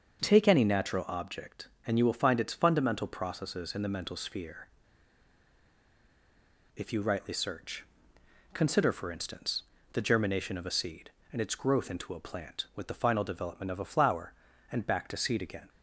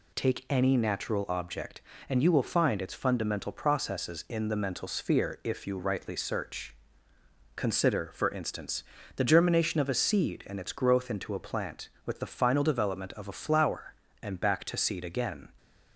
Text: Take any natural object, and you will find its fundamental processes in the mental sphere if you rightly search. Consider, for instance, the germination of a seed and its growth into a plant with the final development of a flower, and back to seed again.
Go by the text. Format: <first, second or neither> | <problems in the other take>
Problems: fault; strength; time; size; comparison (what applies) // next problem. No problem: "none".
second | starts louder than the rest; until 1.2 s; 6.5 dB // pauses between "sphere" and "if"; strong; at 4.6 s; 2.0 s long